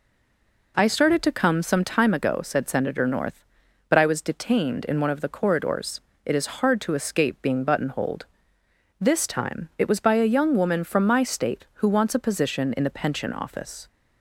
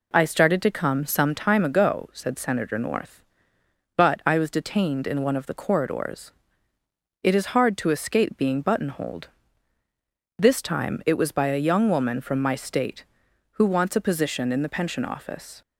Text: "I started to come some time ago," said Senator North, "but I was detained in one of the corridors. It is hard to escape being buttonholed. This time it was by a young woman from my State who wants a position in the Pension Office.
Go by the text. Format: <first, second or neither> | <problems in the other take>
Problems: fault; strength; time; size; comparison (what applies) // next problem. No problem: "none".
second | stays silent before the first word; slight; until 0.7 s; 0.7 s long